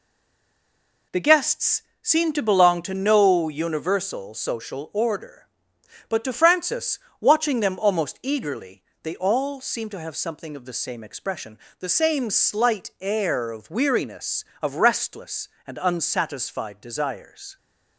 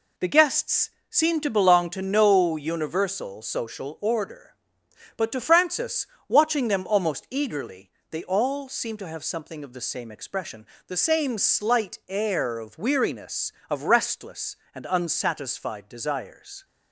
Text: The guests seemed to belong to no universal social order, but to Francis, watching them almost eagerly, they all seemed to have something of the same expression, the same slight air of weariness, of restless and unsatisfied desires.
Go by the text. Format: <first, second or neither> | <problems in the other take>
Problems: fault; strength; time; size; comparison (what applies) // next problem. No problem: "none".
second | stays silent before the first word; until 1.1 s; 1.1 s long // pauses between "guests" and "seemed"; slight; at 1.8 s; 0.22 s long; slight in the second